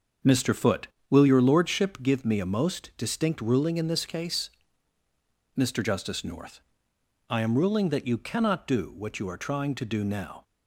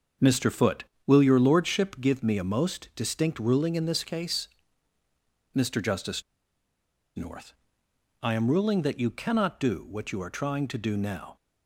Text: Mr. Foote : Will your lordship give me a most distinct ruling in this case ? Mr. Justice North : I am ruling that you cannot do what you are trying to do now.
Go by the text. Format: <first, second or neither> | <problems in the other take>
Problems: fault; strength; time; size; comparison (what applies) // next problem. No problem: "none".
first | starts louder than the rest; until 1.4 s; 6.5 dB; also in the first // pauses between "Justice" and "North"; noticeable; at 6.2 s; 0.95 s long